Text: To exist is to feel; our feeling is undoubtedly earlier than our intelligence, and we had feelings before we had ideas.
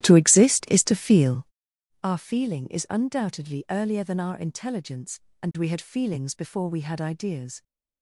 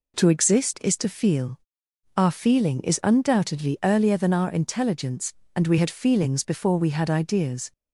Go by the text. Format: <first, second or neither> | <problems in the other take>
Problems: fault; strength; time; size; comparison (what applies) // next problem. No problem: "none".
second | starts louder than the rest; strong; until 1.7 s; 14 dB